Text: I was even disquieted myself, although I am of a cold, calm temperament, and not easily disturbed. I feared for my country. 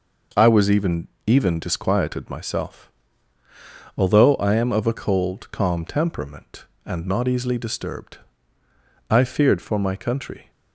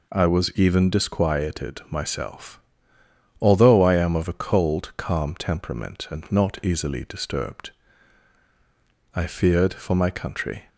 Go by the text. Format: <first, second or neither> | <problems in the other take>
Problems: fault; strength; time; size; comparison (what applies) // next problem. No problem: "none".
second | says "even" twice; at 1.2 s